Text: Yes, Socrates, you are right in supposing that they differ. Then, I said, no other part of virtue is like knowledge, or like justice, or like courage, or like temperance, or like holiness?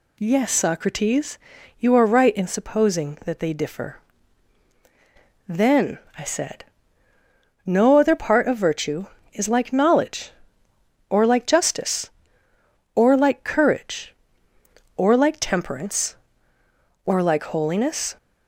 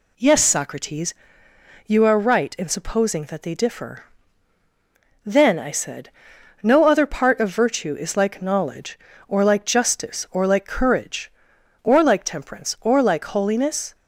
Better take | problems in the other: neither | none

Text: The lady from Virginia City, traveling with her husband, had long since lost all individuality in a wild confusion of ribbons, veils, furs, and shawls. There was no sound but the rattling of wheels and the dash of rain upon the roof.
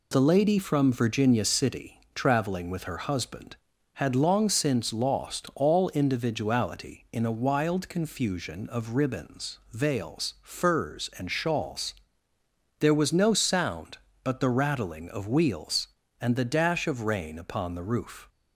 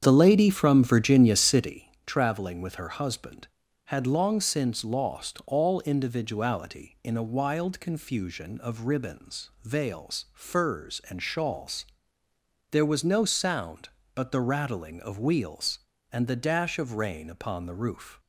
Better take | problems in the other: first | starts louder than the rest; strong; until 1.8 s; 8 dB

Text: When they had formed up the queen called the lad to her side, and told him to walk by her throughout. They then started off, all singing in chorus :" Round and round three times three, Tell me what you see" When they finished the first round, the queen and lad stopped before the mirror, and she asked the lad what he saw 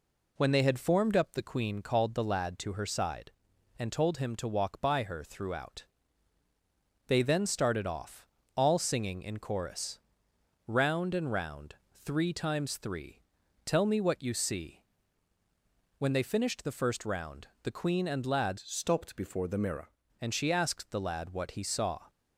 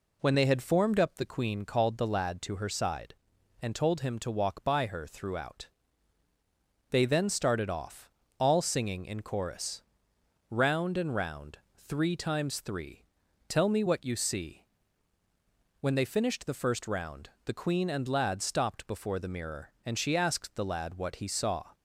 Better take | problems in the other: second | pauses between "round" and "three"; slight; at 11.7 s; 0.18 s long; slight in the second // pauses between "see" and "When"; at 14.8 s; 1.1 s long; also in the second // changes voice from "stopped" to "mirror"; from 18.5 to 19.8 s; 1.3 s long

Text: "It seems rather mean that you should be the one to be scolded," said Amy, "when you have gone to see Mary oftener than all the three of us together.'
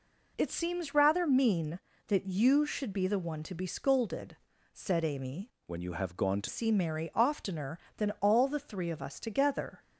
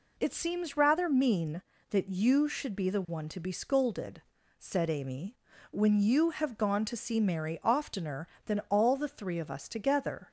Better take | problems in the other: second | changes voice from "when" to "to"; from 5.6 to 6.4 s; 0.8 s long

